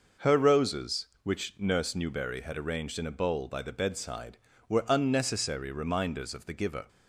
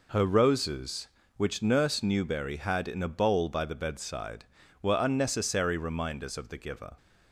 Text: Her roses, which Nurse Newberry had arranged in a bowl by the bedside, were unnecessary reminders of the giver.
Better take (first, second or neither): first